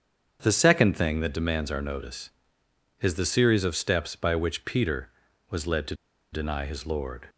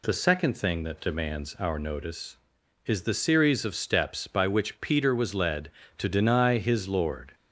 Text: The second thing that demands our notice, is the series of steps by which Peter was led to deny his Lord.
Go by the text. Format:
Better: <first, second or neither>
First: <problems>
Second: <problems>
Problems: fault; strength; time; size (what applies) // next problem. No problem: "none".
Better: second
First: starts louder than the rest; strong; until 1.4 s; 7.5 dB // pauses between "to" and "deny"; at 5.9 s; 0.37 s long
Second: none